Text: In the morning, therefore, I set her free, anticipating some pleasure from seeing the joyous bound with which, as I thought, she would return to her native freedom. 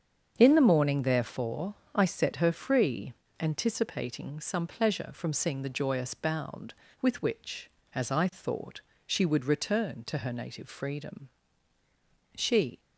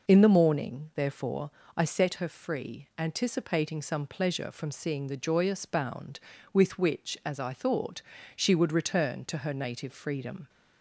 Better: second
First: starts louder than the rest; strong; until 1.3 s; 7 dB // goes on to say "She"; slight; from 12.3 s on; 0.44 s long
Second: none

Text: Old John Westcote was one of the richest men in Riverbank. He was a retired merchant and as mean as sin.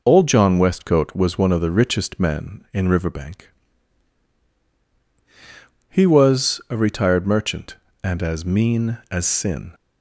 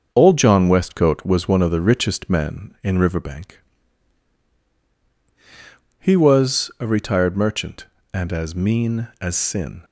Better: first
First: none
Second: gets quieter; throughout; 4 dB

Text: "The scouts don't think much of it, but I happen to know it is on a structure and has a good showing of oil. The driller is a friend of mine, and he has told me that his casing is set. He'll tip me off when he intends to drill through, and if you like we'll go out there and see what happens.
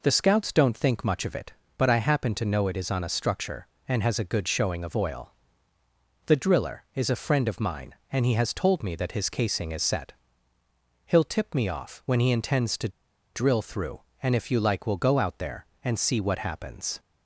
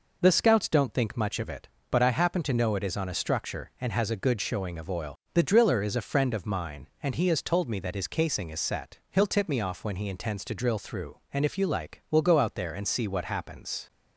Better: second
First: pauses between "to" and "drill"; at 12.8 s; 0.45 s long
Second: none

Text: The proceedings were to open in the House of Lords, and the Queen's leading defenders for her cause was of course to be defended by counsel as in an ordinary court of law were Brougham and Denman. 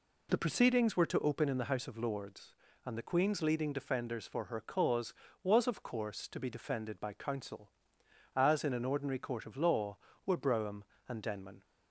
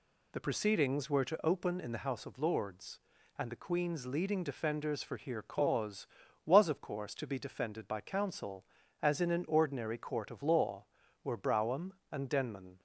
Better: first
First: none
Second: says "here" for "her"; at 5.1 s

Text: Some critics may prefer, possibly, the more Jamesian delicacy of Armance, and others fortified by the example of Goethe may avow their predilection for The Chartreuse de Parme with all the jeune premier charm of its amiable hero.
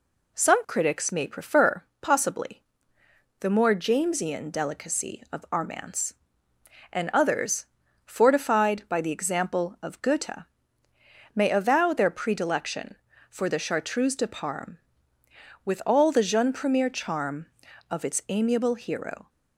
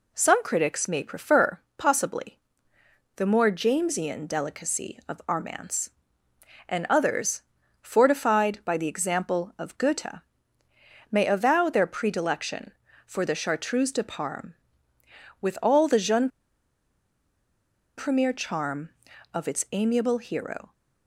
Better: first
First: pauses between "others" and "fortified"; at 7.6 s; 0.40 s long // pauses between "Goethe" and "may"; noticeable; at 10.4 s; 0.90 s long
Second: pauses between "others" and "fortified"; at 7.4 s; 0.40 s long // pauses between "Goethe" and "may"; noticeable; at 10.2 s; 0.90 s long // pauses between "jeune" and "premier"; strong; at 16.2 s; 1.6 s long

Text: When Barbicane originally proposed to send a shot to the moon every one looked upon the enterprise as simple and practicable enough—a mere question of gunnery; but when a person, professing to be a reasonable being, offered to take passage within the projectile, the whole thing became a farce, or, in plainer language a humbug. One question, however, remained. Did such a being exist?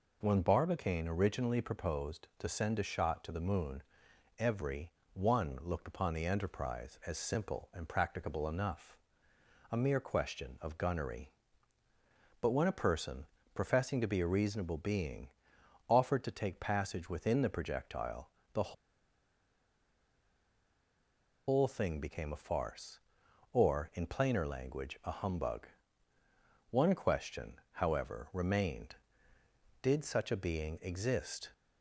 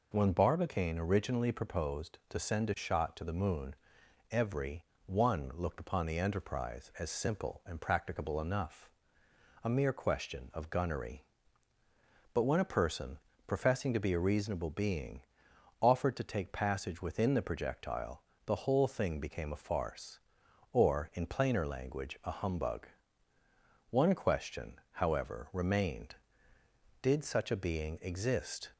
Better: second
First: pauses between "moon" and "every"; noticeable; at 3.8 s; 0.56 s long // pauses between "every" and "one"; slight; at 4.9 s; 0.22 s long // pauses between "the" and "whole"; strong; at 18.7 s; 2.7 s long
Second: pauses between "moon" and "every"; noticeable; at 3.7 s; 0.56 s long // pauses between "every" and "one"; slight; at 4.8 s; 0.22 s long

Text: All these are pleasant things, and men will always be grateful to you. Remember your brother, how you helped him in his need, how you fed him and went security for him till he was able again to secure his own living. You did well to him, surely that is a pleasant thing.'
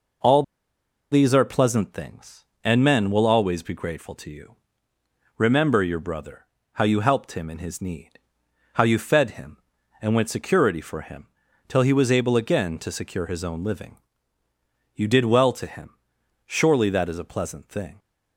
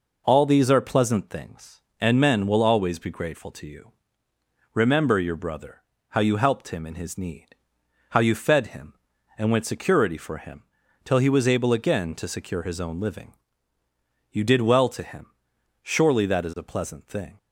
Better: second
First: pauses between "All" and "these"; noticeable; at 0.4 s; 0.67 s long // pauses between "him" and "till"; at 11.2 s; 0.40 s long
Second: pauses between "him" and "till"; at 10.6 s; 0.40 s long

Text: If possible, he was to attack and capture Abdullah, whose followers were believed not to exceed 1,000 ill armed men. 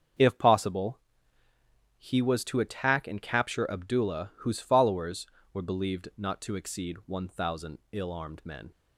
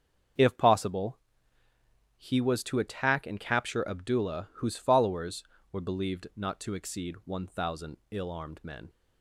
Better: neither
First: starts louder than the rest; until 2.1 s; 7 dB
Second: starts louder than the rest; until 2.3 s; 7 dB

